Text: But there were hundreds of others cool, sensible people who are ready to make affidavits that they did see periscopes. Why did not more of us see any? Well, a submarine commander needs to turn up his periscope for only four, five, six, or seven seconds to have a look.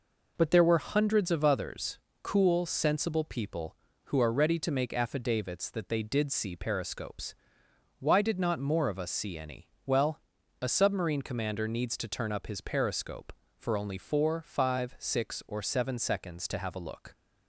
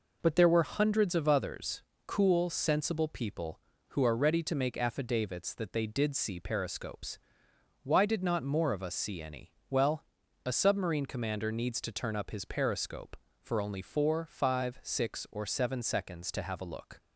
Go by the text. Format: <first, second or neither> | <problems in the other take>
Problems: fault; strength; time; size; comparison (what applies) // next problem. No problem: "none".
neither | pauses between "others" and "cool"; slight; the same in both